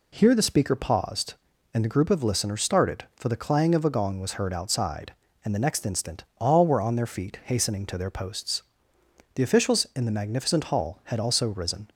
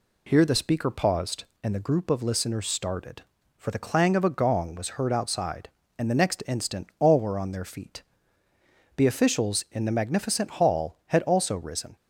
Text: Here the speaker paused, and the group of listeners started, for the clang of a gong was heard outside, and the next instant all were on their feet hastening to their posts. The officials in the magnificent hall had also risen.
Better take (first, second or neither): first